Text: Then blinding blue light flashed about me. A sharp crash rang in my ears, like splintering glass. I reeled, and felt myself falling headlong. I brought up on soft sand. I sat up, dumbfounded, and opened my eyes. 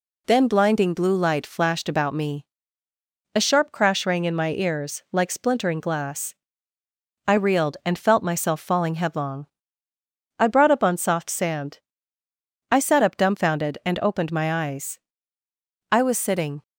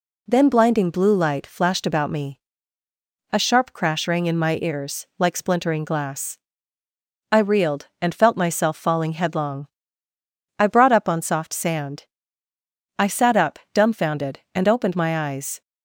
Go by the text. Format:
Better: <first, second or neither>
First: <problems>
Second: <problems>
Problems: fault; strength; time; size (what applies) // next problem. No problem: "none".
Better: second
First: goes on to say "I was sitting"; noticeable; from 15.9 s on; 0.72 s long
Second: none